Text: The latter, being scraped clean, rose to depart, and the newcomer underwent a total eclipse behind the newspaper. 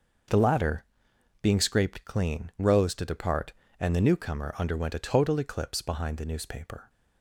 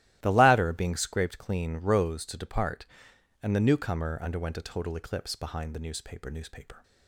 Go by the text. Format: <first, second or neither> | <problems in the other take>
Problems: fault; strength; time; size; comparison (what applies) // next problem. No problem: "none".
first | starts louder than the rest; strong; until 1.2 s; 15 dB; also in the first // says "newspaper" twice; at 6.3 s